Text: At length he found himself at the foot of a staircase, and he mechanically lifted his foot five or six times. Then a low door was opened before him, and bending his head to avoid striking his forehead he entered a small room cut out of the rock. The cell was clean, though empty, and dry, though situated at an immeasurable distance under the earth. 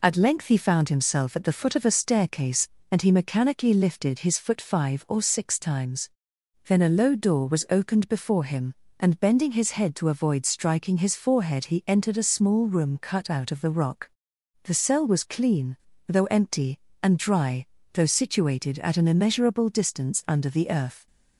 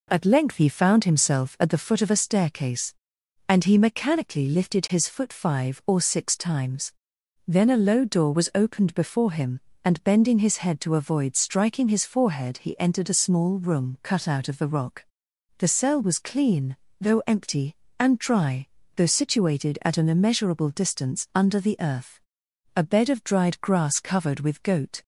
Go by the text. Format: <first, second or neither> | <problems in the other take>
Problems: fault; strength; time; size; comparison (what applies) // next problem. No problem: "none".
first | goes on to say "A bed of dried grass covered with goat"; strong; from 22.7 s on; 2.2 s long